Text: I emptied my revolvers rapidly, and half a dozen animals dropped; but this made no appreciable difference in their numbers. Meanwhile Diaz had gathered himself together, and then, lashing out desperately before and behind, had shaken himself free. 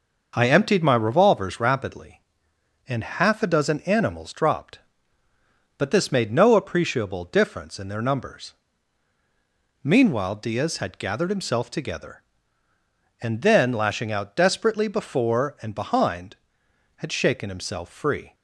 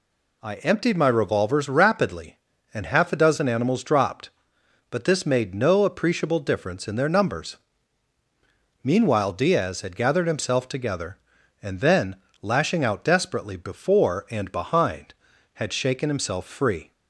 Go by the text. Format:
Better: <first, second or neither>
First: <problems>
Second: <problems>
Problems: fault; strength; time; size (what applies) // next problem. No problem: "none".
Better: neither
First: none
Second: none